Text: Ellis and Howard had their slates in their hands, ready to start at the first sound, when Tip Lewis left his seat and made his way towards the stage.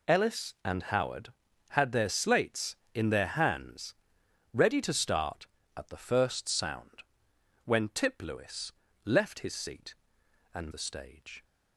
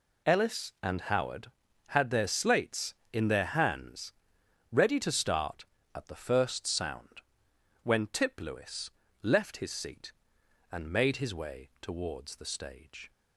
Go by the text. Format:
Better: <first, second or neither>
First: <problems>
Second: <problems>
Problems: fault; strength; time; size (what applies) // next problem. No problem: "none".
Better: second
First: pauses between "Lewis" and "left"; slight; at 8.7 s; 0.32 s long // skips "made his way towards"; at 10.7 s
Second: pauses between "Lewis" and "left"; slight; at 8.9 s; 0.31 s long